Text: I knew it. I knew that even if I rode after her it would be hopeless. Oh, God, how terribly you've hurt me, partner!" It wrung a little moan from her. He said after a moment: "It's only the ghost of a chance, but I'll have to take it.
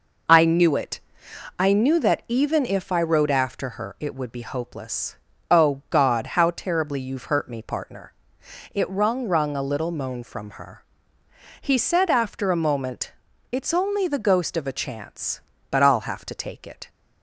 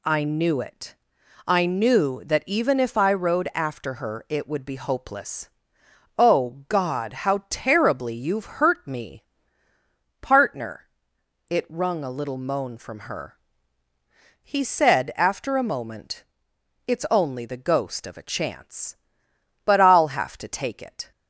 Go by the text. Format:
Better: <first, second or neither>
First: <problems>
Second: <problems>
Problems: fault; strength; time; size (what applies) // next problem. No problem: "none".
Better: second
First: says "wrung" twice; at 9.2 s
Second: none